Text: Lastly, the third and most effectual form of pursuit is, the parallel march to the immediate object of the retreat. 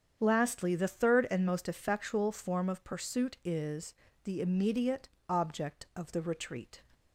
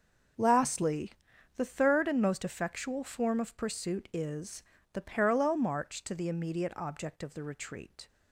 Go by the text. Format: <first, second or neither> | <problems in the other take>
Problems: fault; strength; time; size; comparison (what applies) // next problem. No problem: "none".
second | starts louder than the rest; strong; until 1.2 s; 8 dB; also in the second // skips "parallel march to the"; at 4.4 s // pauses between "immediate" and "object"; slight; at 5.0 s; 0.20 s long